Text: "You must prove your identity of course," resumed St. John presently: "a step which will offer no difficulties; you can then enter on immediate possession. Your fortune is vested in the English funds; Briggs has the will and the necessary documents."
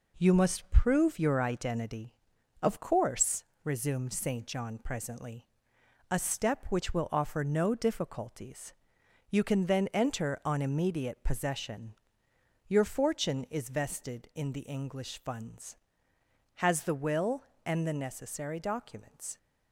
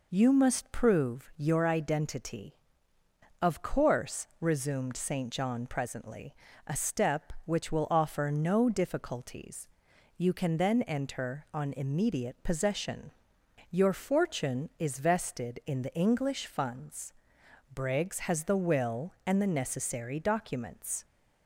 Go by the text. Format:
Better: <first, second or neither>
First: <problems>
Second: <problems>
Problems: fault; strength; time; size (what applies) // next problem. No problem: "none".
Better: second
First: skips "Briggs"; at 16.1 s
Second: none